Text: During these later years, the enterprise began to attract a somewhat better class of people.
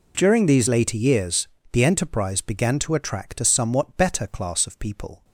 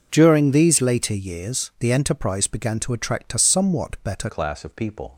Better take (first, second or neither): first